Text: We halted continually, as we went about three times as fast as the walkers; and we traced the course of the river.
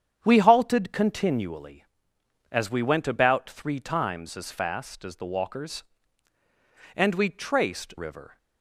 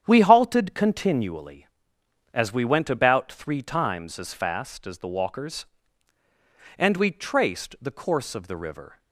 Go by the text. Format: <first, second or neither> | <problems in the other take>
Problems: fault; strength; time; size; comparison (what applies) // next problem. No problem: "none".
second | starts louder than the rest; strong; until 1.2 s; 8.5 dB; strong in the second // skips "the course of the"; at 7.9 s